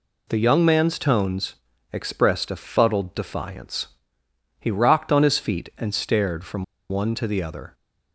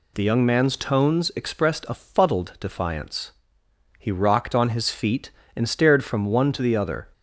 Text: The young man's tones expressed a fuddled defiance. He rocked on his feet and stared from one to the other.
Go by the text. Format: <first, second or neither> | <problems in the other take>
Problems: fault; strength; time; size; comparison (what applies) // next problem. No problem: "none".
second | pauses between "tones" and "expressed"; slight; at 1.5 s; 0.36 s long // pauses between "from" and "one"; slight; at 6.6 s; 0.25 s long